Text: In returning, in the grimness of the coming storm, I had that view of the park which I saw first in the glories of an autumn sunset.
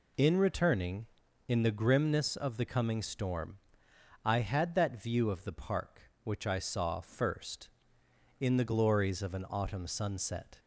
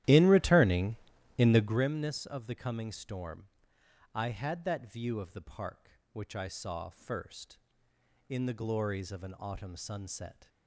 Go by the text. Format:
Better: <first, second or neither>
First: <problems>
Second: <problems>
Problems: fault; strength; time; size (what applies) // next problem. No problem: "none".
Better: first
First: none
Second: starts louder than the rest; strong; until 1.9 s; 13 dB